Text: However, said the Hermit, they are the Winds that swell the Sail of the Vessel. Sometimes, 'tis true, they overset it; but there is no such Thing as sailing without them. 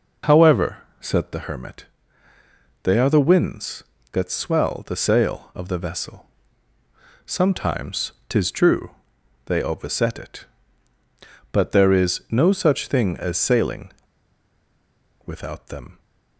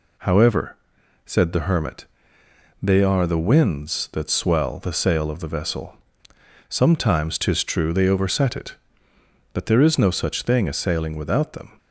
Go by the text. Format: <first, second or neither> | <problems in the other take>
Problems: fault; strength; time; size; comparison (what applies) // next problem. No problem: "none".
second | pauses between "sailing" and "without"; strong; at 13.9 s; 1.3 s long